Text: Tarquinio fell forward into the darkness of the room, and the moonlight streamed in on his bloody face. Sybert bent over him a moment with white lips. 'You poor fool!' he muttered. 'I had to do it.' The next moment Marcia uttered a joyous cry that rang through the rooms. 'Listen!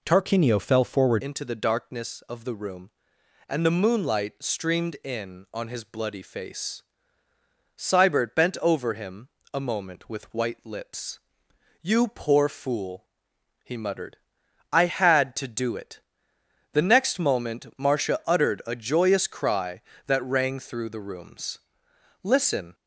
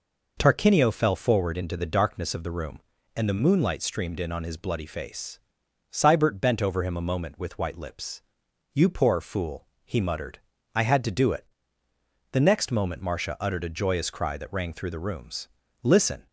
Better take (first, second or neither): second